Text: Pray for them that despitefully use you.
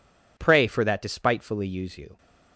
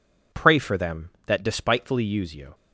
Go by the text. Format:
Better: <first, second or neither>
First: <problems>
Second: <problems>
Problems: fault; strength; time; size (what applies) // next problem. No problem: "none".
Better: second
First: skips "them"; at 0.8 s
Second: none